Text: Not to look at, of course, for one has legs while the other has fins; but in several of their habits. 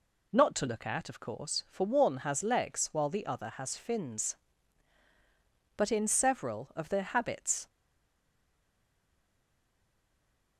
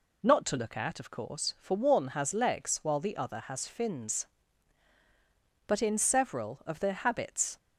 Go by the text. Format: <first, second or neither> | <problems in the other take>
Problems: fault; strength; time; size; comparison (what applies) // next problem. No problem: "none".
second | stays silent after the last word; strong; from 7.6 s on; 2.9 s long